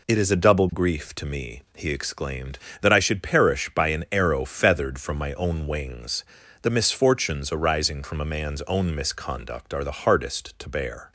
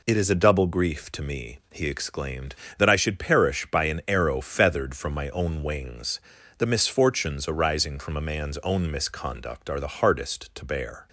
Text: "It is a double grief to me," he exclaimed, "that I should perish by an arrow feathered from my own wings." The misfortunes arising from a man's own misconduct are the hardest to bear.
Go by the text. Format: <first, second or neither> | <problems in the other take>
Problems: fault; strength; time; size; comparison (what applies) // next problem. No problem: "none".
neither | none